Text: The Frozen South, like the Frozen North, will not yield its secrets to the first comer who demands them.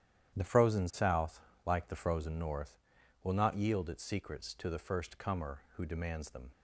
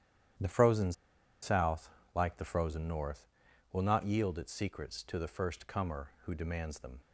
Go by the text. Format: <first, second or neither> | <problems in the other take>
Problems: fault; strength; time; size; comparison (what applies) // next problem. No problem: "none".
first | starts louder than the rest; strong; until 1.8 s; 10.5 dB; strong in the first // pauses between "Frozen" and "South"; noticeable; at 0.9 s; 0.49 s long